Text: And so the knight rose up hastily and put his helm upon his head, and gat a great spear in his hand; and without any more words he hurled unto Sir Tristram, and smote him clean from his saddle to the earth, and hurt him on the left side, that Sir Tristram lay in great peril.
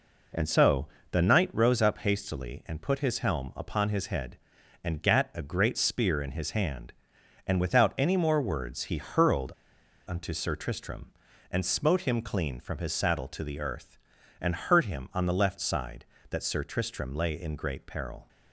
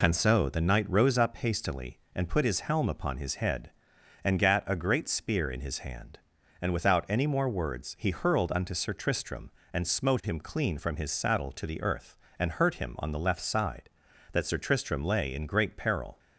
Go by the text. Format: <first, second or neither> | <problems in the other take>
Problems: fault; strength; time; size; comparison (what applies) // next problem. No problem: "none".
second | pauses between "so" and "the"; slight; at 0.8 s; 0.24 s long // pauses between "hurled" and "unto"; noticeable; at 9.5 s; 0.56 s long